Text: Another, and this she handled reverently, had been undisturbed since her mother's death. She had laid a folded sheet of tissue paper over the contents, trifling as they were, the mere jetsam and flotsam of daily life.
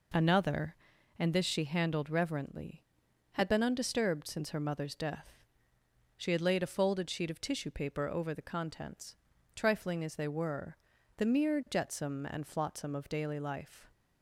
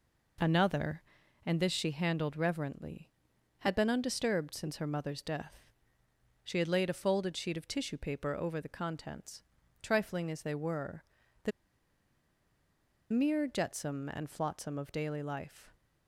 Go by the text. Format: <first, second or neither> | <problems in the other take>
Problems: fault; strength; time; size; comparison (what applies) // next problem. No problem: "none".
first | pauses between "the" and "mere"; strong; at 11.5 s; 1.5 s long